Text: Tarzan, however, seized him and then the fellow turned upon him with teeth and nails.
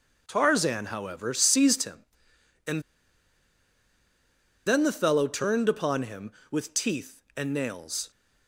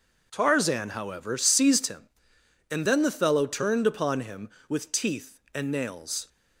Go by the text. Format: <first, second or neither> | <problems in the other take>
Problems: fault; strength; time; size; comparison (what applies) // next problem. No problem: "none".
second | starts louder than the rest; noticeable; until 1.2 s; 6 dB // pauses between "and" and "then"; strong; at 2.8 s; 1.8 s long